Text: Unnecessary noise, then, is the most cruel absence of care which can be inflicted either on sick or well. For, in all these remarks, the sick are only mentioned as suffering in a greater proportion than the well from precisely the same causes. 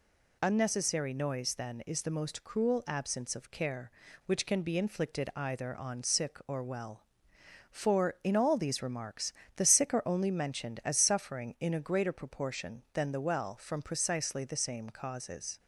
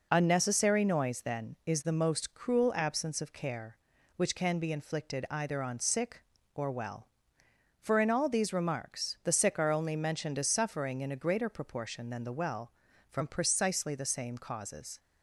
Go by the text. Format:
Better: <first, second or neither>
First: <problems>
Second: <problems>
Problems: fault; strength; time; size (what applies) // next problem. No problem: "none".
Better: neither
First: none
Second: none